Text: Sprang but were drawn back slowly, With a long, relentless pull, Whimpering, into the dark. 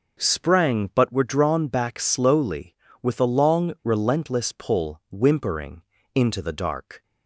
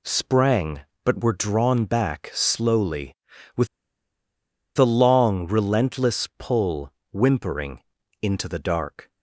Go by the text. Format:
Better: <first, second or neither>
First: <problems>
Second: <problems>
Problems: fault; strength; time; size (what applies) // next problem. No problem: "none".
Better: first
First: none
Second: pauses between "With" and "a"; at 3.6 s; 1.1 s long